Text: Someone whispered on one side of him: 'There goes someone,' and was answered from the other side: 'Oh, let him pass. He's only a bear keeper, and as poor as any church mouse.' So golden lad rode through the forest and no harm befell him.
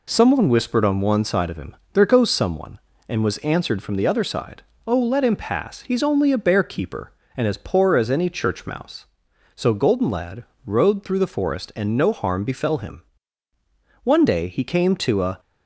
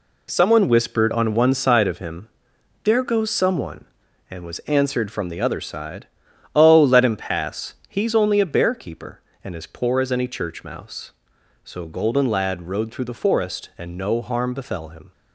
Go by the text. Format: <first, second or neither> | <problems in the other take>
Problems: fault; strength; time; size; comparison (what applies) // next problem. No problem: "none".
second | pauses between "lad" and "rode"; slight; at 10.4 s; 0.20 s long // goes on to say "One day he came to a"; from 14.0 s on; 1.3 s long